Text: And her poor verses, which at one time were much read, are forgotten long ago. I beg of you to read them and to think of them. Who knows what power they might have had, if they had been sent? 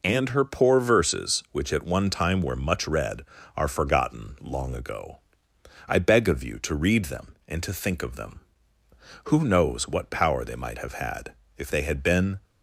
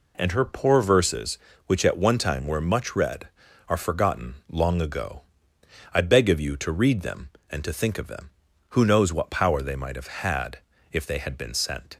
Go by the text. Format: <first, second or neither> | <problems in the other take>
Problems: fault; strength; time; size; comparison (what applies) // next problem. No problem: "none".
second | stops before "sent"; at 12.4 s